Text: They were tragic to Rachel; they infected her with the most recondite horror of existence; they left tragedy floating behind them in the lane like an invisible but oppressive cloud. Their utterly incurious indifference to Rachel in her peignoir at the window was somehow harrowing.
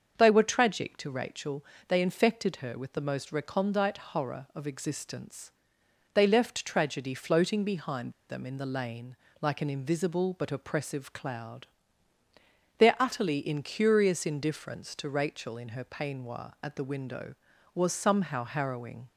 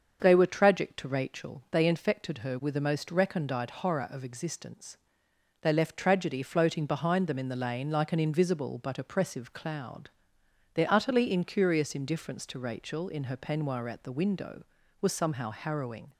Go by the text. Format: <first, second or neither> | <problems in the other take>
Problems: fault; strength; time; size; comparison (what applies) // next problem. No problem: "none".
second | starts louder than the rest; until 1.2 s; 6.5 dB; also in the second // pauses between "behind" and "them"; slight; at 8.1 s; 0.17 s long // pauses between "lane" and "like"; slight; at 9.1 s; 0.26 s long